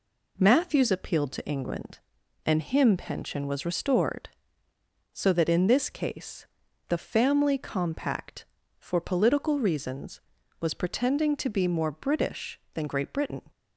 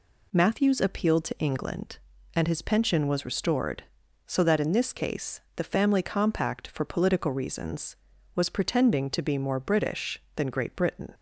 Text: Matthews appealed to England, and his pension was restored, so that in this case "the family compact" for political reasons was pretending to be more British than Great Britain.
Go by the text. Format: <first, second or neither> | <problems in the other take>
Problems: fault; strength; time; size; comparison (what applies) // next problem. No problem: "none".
second | says "him" for "his"; at 2.6 s // pauses between "case" and "the"; at 6.4 s; 0.44 s long; slight in the second